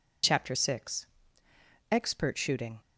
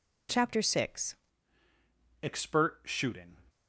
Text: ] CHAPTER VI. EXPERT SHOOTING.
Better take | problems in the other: first | changes voice at "EXPERT"; from 2.2 s on; 1.1 s long

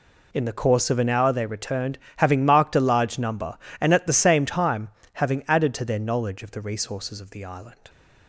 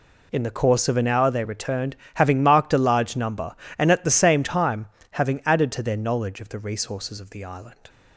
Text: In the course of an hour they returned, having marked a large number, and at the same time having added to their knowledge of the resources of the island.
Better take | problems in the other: neither | pauses between "time" and "having"; slight; the same in both

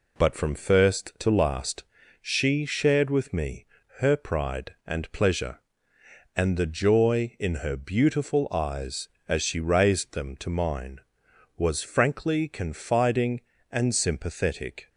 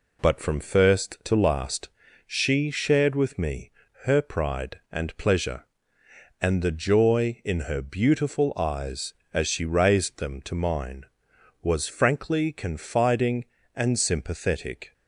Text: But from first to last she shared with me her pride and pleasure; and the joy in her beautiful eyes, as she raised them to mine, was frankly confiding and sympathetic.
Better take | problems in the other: neither | pauses between "last" and "she"; the same in both // pauses between "me" and "her"; slight; the same in both

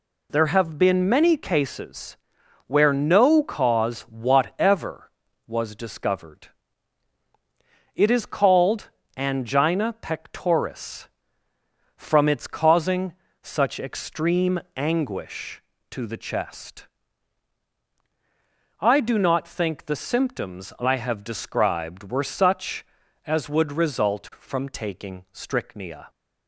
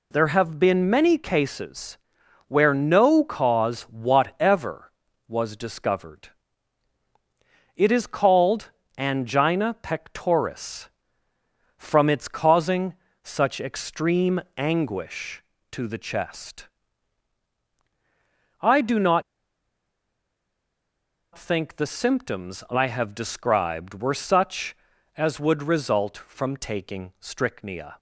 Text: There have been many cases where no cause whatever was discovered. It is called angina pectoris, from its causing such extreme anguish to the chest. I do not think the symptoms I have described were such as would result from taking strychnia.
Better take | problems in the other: first | pauses between "cases" and "where"; noticeable; at 1.9 s; 0.52 s long; noticeable in the first // pauses between "called" and "angina"; slight; at 8.7 s; 0.26 s long; slight in the first // pauses between "causing" and "such"; slight; at 12.9 s; 0.30 s long; slight in the first // pauses between "extreme" and "anguish"; slight; at 14.4 s; 0.16 s long; slight in the first // pauses between "not" and "think"; strong; at 19.2 s; 2.1 s long

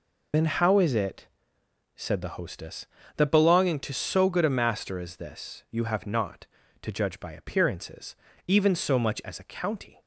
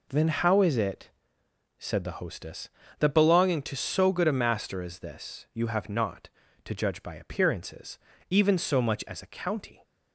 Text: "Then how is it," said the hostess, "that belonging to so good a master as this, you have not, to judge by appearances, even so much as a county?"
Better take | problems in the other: second | loses the start of "Then"; at 0.3 s; 70 ms

